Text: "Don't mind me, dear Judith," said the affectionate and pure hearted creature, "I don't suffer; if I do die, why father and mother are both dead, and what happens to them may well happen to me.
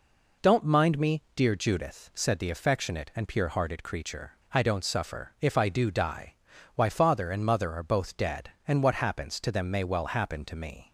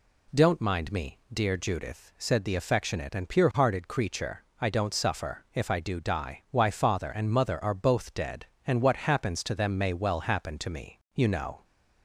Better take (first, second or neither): first